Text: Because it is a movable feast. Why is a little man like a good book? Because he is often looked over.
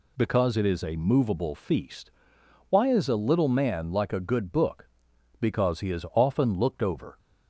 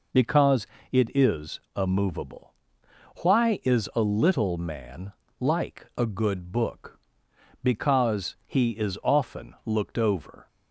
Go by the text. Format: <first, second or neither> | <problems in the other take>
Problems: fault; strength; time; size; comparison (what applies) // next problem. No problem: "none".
first | pauses between "Because" and "it"; slight; at 0.6 s; 0.26 s long // pauses between "is" and "a"; slight; at 1.5 s; 0.16 s long // skips "feast"; at 2.8 s // pauses between "man" and "like"; slight; at 5.1 s; 0.26 s long